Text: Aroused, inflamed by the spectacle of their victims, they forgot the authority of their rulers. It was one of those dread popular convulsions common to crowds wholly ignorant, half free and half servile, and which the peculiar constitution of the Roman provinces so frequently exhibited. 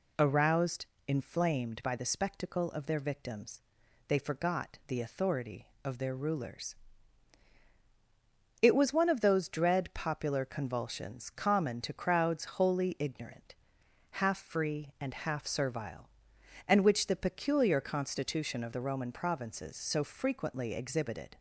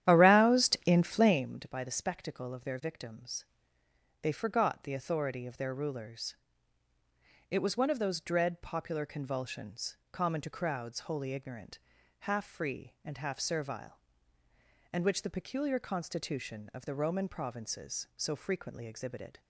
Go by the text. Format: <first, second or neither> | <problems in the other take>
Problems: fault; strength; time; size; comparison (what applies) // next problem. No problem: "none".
first | starts louder than the rest; strong; until 1.4 s; 11 dB // pauses between "convulsions" and "common"; slight; at 9.9 s; 0.16 s long